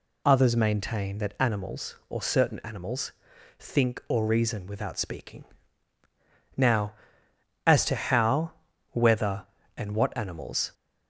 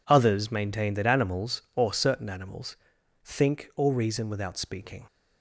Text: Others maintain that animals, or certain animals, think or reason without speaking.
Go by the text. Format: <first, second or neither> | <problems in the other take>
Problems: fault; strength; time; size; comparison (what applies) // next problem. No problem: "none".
second | goes on to say "Now as to how whether and what animals"; strong; from 6.5 s on; 4.1 s long